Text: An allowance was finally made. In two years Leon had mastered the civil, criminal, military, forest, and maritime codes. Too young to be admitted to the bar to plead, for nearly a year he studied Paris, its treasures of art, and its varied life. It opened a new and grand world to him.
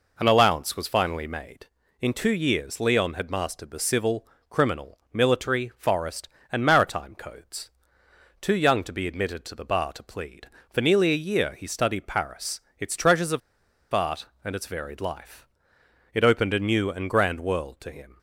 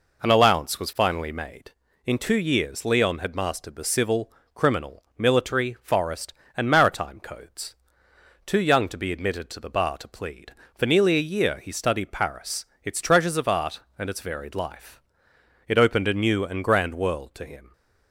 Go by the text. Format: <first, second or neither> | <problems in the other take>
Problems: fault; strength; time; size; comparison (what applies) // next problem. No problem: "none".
second | pauses between "of" and "art"; noticeable; at 13.4 s; 0.53 s long